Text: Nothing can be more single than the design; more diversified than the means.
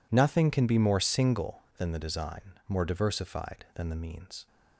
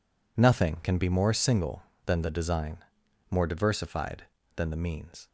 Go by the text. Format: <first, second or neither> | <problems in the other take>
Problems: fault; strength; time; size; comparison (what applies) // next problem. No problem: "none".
neither | none